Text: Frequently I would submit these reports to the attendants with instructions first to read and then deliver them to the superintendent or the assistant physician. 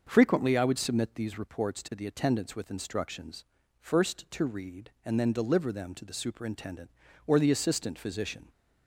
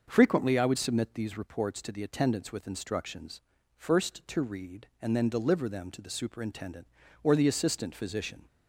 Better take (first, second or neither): neither